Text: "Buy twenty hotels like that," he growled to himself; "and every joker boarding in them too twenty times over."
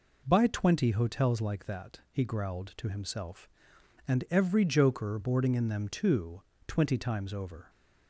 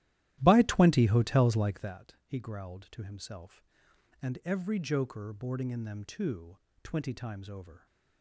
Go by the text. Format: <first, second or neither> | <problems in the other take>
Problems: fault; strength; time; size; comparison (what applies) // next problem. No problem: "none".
first | starts louder than the rest; strong; until 2.0 s; 14 dB // pauses between "too" and "twenty"; slight; at 6.5 s; 0.24 s long; slight in the first